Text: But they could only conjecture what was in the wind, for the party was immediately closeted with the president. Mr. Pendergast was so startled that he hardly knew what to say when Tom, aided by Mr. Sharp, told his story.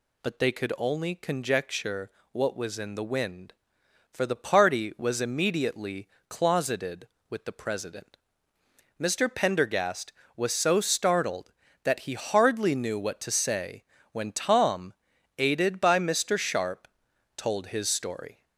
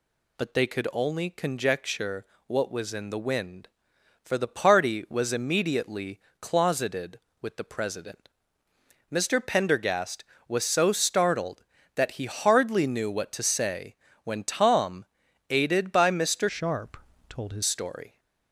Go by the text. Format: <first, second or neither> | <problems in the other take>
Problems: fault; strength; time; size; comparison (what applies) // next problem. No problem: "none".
first | pauses between "conjecture" and "what"; slight; at 2.2 s; 0.22 s long; slight in the first // pauses between "immediately" and "closeted"; slight; at 6.1 s; 0.22 s long; slight in the first // pauses between "say" and "when"; slight; at 13.9 s; 0.28 s long; slight in the first // changes voice from "Sharp" to "his"; from 16.4 to 17.6 s; 1.2 s long